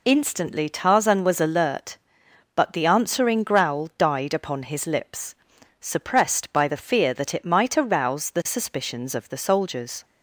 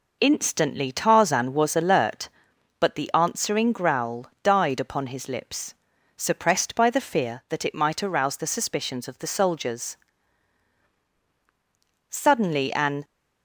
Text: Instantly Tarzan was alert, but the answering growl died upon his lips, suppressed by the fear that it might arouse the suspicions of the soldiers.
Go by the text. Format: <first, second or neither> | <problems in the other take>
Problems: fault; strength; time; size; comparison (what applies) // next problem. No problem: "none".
first | pauses between "growl" and "died"; slight; at 4.2 s; 0.16 s long // goes on to say "Suddenly an"; noticeable; from 12.0 s on; 0.94 s long